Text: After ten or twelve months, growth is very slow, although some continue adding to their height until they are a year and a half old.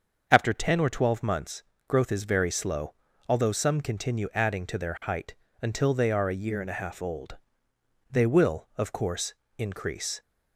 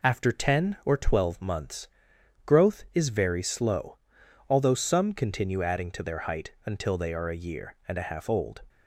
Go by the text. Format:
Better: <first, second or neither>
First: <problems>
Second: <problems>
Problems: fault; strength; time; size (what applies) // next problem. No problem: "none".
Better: second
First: starts louder than the rest; until 1.2 s; 6.5 dB // pauses between "height" and "until"; slight; at 5.3 s; 0.26 s long // goes on to say "They will of course increase"; strong; from 8.0 s on; 2.1 s long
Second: none